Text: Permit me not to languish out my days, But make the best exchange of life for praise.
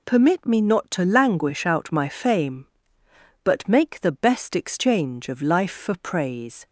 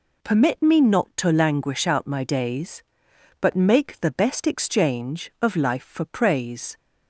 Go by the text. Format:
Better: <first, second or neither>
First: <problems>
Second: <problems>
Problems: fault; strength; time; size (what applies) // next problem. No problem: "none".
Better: second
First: says "fame" for "days"; at 2.0 s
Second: none